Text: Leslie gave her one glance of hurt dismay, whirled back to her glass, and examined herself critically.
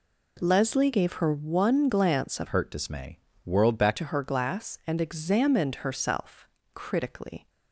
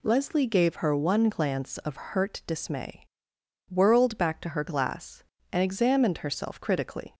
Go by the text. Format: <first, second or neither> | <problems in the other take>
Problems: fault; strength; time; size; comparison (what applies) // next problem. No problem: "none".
second | changes voice from "hurt" to "back"; from 2.4 to 3.9 s; 1.5 s long // pauses between "herself" and "critically"; slight; at 6.4 s; 0.26 s long